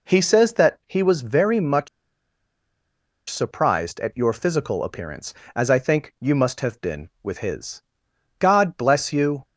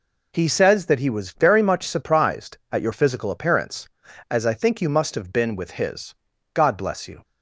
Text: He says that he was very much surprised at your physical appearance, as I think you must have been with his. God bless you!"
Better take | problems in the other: second | pauses between "much" and "surprised"; strong; at 1.8 s; 1.4 s long

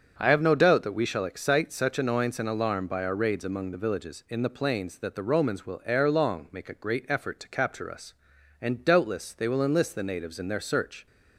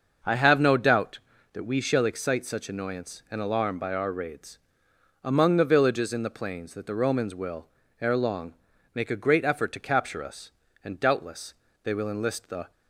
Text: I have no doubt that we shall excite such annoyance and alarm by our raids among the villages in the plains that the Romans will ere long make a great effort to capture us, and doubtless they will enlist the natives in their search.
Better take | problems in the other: first | starts louder than the rest; noticeable; until 1.6 s; 6 dB; also in the first // pauses between "raids" and "among"; noticeable; at 4.5 s; 0.64 s long // pauses between "will" and "ere"; slight; at 7.6 s; 0.32 s long // pauses between "long" and "make"; at 8.5 s; 0.40 s long // pauses between "doubtless" and "they"; slight; at 11.5 s; 0.30 s long // stops before "natives in their search"; at 12.7 s

